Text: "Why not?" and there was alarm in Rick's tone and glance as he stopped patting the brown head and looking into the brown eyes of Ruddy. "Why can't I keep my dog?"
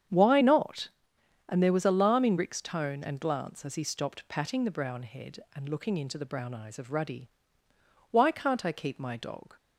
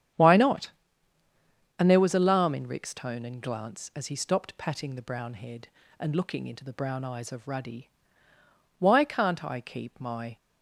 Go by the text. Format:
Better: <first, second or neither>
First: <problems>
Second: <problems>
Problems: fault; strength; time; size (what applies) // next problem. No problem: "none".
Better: first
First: starts louder than the rest; strong; until 1.7 s; 8.5 dB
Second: starts louder than the rest; strong; until 2.2 s; 9 dB // stops before "dog"; at 10.3 s